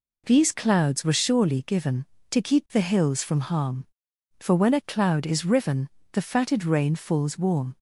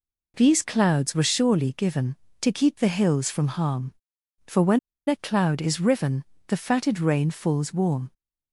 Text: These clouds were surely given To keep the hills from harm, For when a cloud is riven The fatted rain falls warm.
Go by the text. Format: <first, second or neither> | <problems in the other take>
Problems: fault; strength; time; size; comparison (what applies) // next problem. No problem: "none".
first | pauses between "when" and "a"; slight; at 4.7 s; 0.29 s long // pauses between "riven" and "The"; slight; at 6.2 s; 0.24 s long; slight in the first